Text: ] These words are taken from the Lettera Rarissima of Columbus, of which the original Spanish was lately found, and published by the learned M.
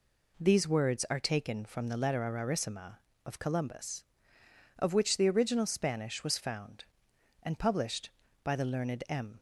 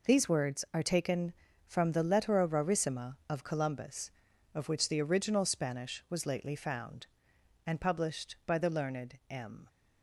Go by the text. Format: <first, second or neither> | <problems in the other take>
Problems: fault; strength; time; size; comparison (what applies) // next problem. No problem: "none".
second | skips "lately"; at 6.3 s